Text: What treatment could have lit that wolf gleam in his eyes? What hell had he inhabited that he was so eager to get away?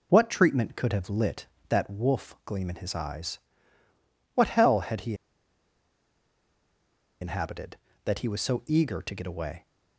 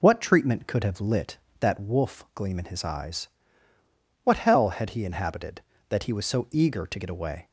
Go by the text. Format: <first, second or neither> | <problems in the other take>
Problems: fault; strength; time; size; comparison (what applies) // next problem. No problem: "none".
second | pauses between "he" and "inhabited"; strong; at 5.1 s; 2.0 s long